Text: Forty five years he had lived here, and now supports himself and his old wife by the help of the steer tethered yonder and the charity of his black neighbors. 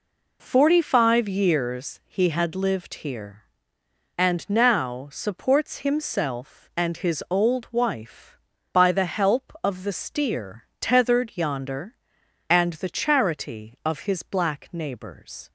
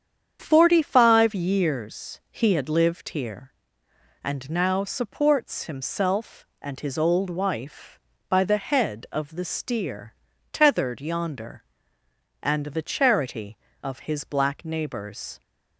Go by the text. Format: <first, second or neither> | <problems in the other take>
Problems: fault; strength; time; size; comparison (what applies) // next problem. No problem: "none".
first | starts louder than the rest; strong; until 1.4 s; 8 dB // says "head" for "help"; at 8.5 s // pauses between "steer" and "tethered"; slight; at 10.1 s; 0.36 s long; slight in the first